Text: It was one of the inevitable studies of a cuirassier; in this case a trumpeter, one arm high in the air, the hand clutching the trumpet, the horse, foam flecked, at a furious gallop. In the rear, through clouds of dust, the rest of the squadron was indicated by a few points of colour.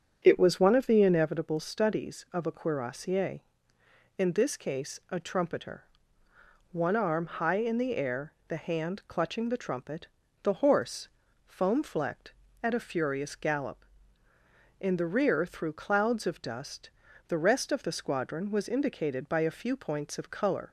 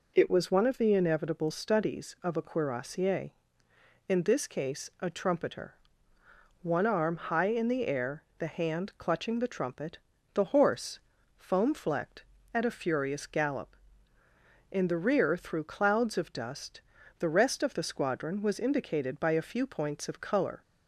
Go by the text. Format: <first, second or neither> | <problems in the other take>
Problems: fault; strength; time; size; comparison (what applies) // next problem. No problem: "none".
second | starts louder than the rest; strong; until 1.4 s; 8 dB